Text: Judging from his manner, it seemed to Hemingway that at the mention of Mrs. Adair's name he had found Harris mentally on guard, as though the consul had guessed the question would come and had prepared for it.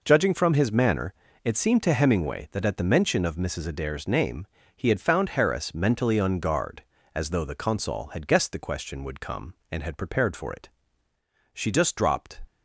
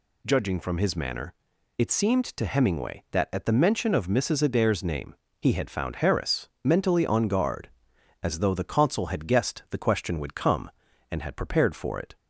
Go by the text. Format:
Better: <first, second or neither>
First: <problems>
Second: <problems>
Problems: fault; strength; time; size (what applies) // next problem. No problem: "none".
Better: second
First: pauses between "name" and "he"; slight; at 4.4 s; 0.28 s long // goes on to say "She just dropped"; noticeable; from 11.5 s on; 0.88 s long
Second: pauses between "name" and "he"; slight; at 5.1 s; 0.24 s long